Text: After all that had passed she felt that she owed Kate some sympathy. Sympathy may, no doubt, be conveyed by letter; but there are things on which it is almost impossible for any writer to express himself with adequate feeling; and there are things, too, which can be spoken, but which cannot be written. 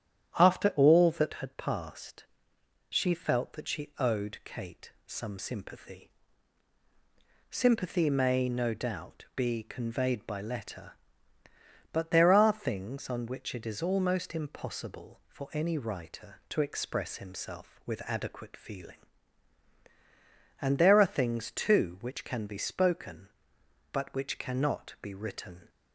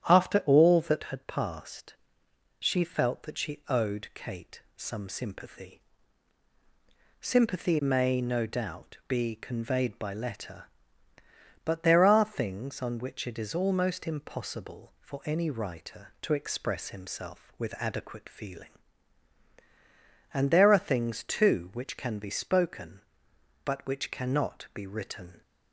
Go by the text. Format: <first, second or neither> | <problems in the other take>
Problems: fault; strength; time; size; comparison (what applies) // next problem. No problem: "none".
neither | starts louder than the rest; strong; the same in both // pauses between "passed" and "she"; noticeable; the same in both // pauses between "Kate" and "some"; slight; the same in both